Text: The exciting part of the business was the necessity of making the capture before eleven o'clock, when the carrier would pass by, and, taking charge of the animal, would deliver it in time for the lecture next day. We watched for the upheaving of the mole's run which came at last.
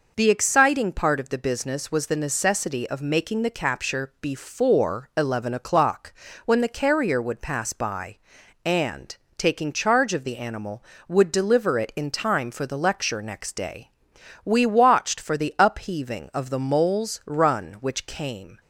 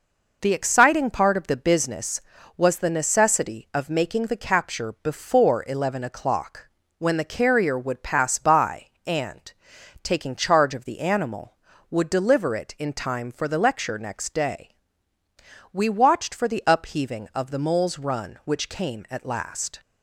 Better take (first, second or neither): second